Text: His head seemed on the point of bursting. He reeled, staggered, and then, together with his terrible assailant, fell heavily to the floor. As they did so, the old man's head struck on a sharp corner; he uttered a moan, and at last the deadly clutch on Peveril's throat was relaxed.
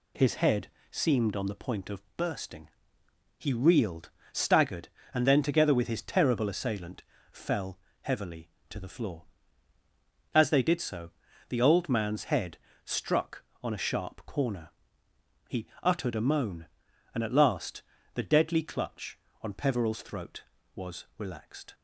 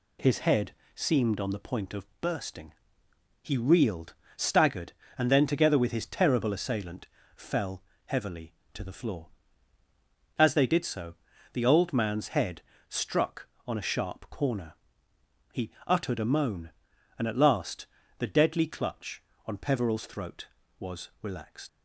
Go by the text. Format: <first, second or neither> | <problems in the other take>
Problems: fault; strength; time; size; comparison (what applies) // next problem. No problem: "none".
first | pauses between "head" and "seemed"; slight; at 0.7 s; 0.22 s long; slight in the first // pauses between "fell" and "heavily"; slight; at 7.8 s; 0.22 s long; slight in the first // pauses between "head" and "struck"; slight; at 12.6 s; 0.30 s long; slight in the first // pauses between "he" and "uttered"; slight; at 15.7 s; 0.16 s long; slight in the first // pauses between "last" and "the"; slight; at 17.8 s; 0.32 s long; slight in the first // leaves "relaxed" unfinished; at 21.6 s; 90 ms